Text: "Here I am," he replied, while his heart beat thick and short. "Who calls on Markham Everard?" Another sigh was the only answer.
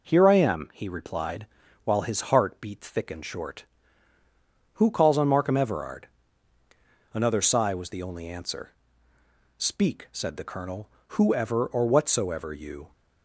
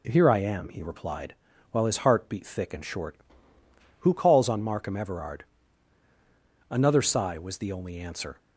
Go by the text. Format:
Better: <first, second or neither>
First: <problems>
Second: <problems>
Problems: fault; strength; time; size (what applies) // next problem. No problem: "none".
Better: second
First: goes on to say "Speak said the Colonel whoever or whatsoever you"; strong; from 9.5 s on; 3.3 s long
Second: none